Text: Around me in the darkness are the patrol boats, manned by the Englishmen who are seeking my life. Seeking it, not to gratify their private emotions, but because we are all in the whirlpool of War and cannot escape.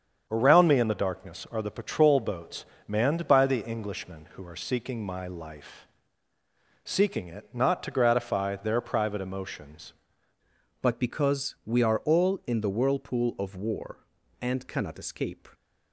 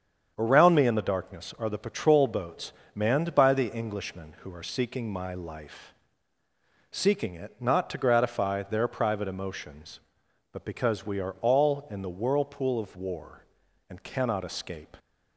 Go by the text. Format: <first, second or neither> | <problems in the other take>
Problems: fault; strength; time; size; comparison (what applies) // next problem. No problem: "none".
second | starts louder than the rest; strong; until 1.3 s; 7.5 dB; strong in the second // changes voice at "but"; from 10.8 s on; 4.6 s long